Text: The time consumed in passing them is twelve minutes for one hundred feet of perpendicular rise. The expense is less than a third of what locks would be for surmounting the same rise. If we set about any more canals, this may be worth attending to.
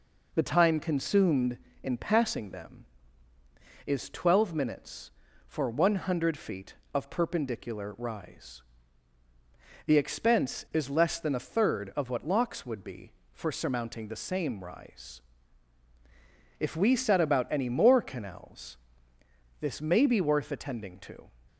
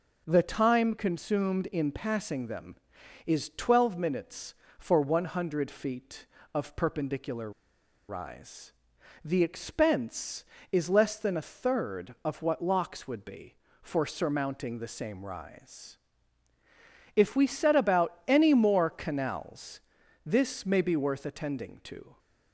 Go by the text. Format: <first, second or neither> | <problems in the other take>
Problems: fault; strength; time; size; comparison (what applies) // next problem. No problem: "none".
first | pauses between "perpendicular" and "rise"; noticeable; at 7.5 s; 0.58 s long